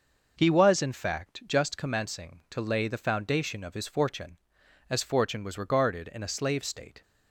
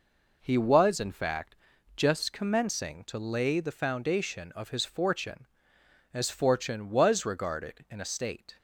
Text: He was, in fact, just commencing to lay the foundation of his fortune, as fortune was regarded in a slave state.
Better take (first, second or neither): first